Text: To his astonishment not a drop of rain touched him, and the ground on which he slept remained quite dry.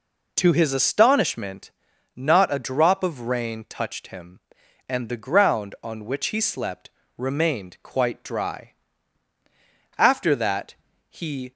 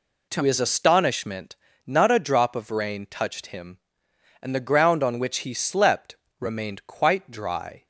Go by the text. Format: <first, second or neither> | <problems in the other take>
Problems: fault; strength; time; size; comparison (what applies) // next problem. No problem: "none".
second | pauses between "astonishment" and "not"; at 1.7 s; 0.42 s long; slight in the second // pauses between "slept" and "remained"; slight; at 6.8 s; 0.26 s long; slight in the second // goes on to say "After that he"; from 9.9 s on; 1.5 s long